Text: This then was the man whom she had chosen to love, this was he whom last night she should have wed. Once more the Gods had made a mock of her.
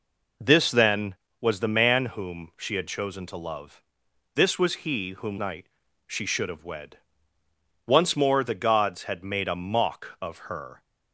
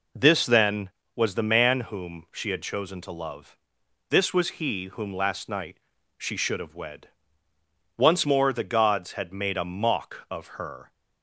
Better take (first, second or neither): second